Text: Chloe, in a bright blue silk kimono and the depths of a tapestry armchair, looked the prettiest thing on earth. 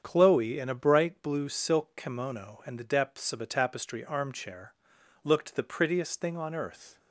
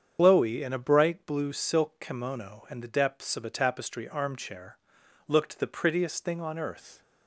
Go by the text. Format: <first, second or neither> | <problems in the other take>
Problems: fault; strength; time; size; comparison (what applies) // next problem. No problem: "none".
first | loses the start of "Chloe"; at 0.1 s; 120 ms // starts louder than the rest; strong; until 1.2 s; 7.5 dB; strong in the first